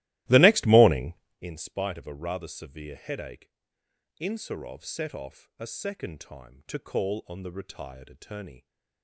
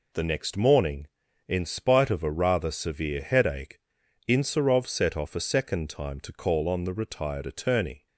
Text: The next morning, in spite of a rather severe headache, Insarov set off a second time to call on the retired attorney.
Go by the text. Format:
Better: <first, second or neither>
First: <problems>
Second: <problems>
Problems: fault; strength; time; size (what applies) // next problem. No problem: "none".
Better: second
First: starts louder than the rest; strong; until 1.5 s; 17 dB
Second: none